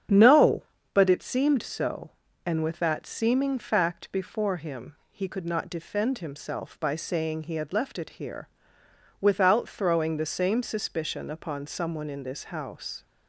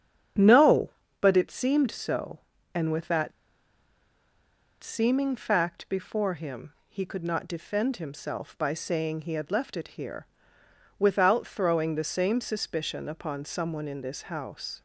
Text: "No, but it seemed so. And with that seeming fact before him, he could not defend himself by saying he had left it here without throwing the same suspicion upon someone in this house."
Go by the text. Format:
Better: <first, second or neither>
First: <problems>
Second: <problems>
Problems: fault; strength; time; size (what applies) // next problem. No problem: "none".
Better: first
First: starts louder than the rest; strong; until 1.3 s; 8 dB // pauses between "here" and "without"; noticeable; at 8.4 s; 0.72 s long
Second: starts louder than the rest; strong; until 1.6 s; 8 dB // pauses between "that" and "seeming"; strong; at 3.3 s; 1.4 s long // pauses between "here" and "without"; noticeable; at 10.2 s; 0.72 s long